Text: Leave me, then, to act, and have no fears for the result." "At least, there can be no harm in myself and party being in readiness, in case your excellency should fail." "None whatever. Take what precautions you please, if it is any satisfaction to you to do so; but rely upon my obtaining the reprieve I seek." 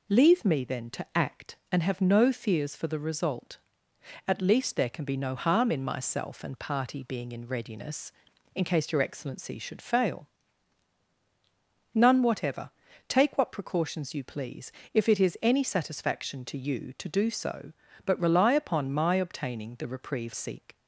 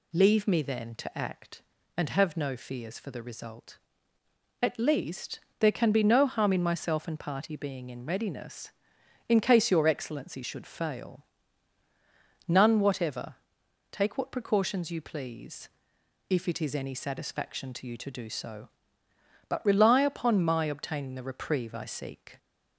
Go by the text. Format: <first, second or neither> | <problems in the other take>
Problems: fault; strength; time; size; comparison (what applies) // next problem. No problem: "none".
second | skips "I"; at 20.3 s